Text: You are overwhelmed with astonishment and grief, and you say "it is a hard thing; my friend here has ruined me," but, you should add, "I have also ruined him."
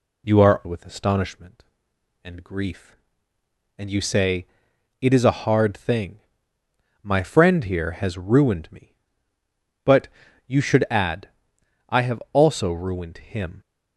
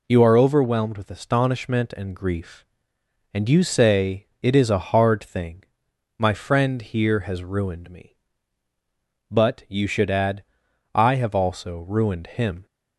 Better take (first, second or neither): second